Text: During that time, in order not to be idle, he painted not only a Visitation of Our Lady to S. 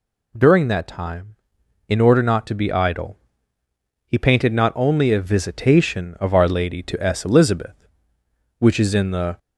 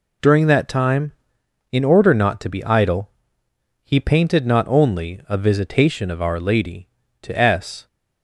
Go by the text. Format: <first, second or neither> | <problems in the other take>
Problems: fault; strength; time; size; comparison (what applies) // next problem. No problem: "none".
second | goes on to say "Elizabeth which is in the"; strong; from 7.2 s on; 2.1 s long